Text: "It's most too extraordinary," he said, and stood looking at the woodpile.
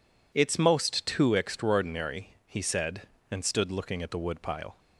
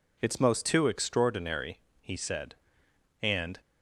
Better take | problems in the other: first | stops before "stood looking at the woodpile"; at 3.5 s

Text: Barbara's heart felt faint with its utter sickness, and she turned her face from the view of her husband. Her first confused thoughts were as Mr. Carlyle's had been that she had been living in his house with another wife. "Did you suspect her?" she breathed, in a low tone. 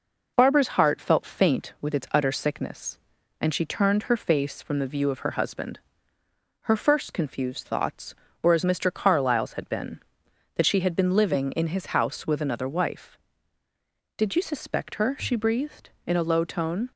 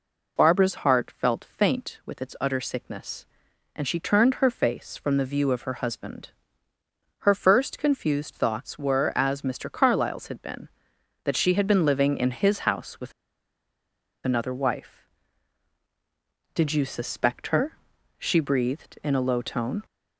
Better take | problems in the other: first | pauses between "with" and "another"; at 13.1 s; 1.1 s long

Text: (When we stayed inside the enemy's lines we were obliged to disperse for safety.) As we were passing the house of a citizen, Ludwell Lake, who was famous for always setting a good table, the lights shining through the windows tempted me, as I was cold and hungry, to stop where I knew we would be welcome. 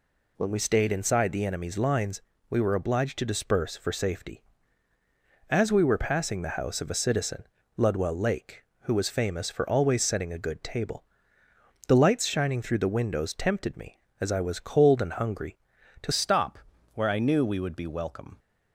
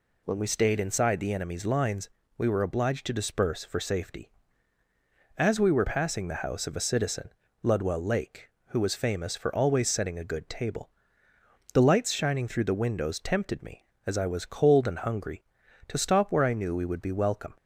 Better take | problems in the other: second | pauses between "lines" and "we"; slight; at 2.2 s; 0.30 s long; slight in the second // changes voice at "stop"; from 16.1 s on; 2.2 s long // pauses between "stop" and "where"; at 16.5 s; 0.38 s long

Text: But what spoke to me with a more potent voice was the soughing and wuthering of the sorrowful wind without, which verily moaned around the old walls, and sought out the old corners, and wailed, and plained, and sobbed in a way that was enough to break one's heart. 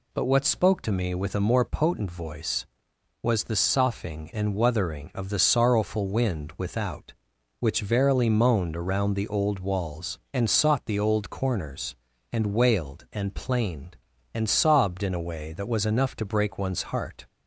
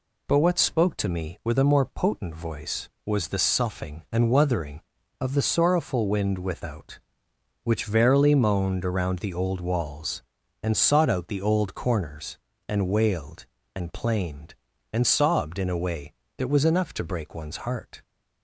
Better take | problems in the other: second | skips "out"; at 10.8 s

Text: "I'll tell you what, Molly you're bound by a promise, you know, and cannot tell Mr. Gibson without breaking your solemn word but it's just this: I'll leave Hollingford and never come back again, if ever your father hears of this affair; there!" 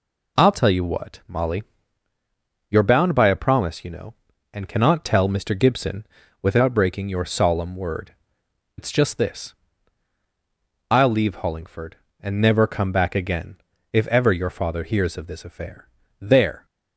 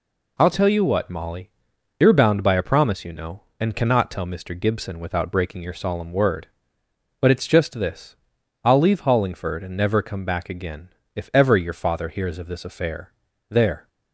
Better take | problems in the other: second | pauses between "Molly" and "you're"; at 1.6 s; 1.0 s long; noticeable in the second // pauses between "Gibson" and "without"; slight; at 6.0 s; 0.36 s long // skips "but"; at 8.4 s

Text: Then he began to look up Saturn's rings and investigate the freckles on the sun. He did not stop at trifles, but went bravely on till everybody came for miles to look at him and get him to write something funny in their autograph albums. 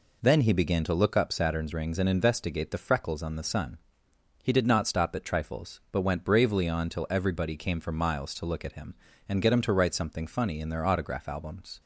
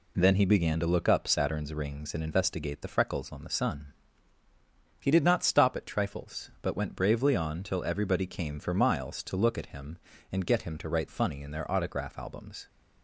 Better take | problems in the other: first | skips "something"; at 11.0 s

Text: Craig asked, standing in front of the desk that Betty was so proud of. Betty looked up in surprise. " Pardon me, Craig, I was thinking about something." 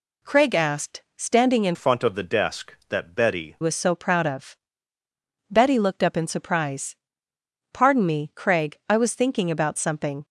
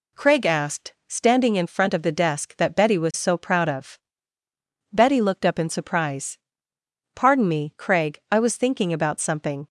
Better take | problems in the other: second | changes voice from "front" to "Betty"; from 1.7 to 3.5 s; 1.8 s long

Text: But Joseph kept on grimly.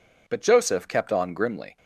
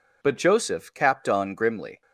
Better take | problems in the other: first | says "capped" for "kept"; at 0.9 s

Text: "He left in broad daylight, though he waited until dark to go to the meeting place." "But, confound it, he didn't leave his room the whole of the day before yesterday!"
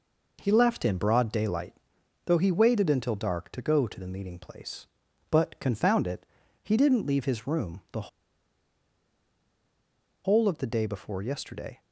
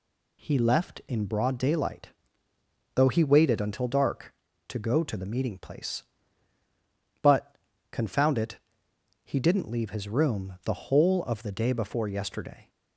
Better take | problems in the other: second | pauses between "the" and "whole"; strong; at 8.0 s; 2.1 s long

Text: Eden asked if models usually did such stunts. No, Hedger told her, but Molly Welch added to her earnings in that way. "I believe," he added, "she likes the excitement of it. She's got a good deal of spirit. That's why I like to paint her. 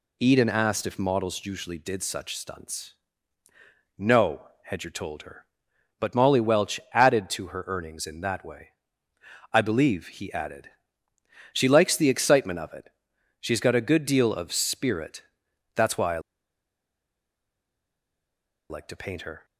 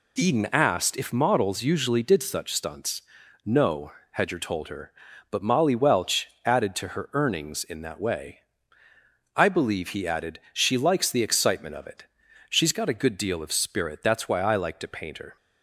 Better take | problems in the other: second | pauses between "I" and "like"; strong; at 16.1 s; 2.5 s long

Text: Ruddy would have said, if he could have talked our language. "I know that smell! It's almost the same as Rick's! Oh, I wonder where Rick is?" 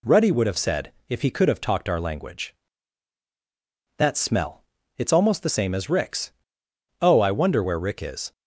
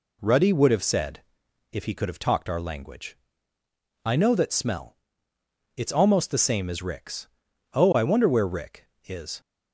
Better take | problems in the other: second | skips "I know"; at 3.2 s

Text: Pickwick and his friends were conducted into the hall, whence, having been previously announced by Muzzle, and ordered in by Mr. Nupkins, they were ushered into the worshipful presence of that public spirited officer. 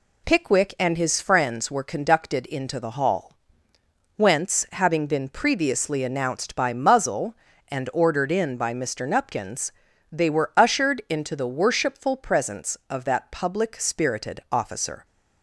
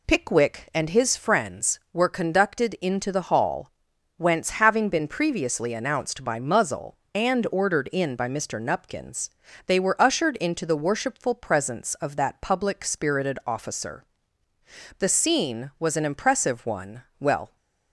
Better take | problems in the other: first | goes on to say "The scene was an impressive one well"; strong; from 14.9 s on; 2.5 s long

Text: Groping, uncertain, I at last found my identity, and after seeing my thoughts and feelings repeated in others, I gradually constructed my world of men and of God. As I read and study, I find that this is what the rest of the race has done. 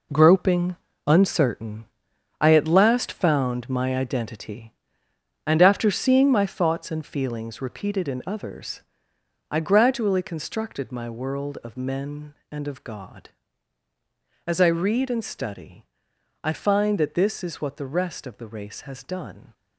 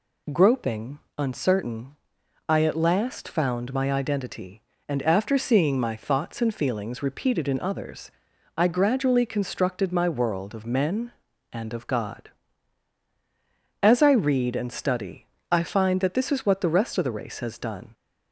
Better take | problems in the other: second | gets quieter; strong; throughout; 9.5 dB

